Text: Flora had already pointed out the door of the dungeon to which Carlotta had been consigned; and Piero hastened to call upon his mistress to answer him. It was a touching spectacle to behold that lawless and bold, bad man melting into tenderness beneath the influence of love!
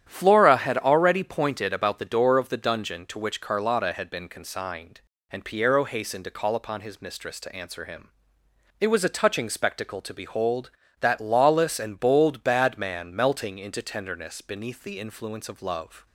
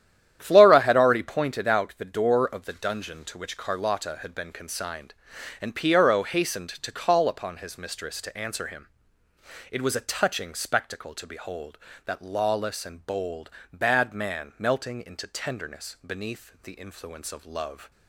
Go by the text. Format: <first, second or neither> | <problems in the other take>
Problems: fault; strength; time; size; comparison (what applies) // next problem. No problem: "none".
second | starts louder than the rest; strong; until 1.0 s; 10.5 dB; strong in the second // says "about" for "out"; at 1.7 s